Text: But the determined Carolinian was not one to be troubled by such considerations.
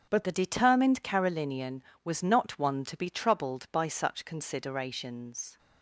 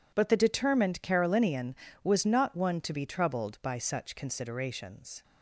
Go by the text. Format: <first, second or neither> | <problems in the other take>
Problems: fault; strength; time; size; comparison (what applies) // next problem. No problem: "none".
second | starts louder than the rest; strong; until 1.1 s; 8 dB // changes voice at "the"; from 0.2 s on; 5.3 s long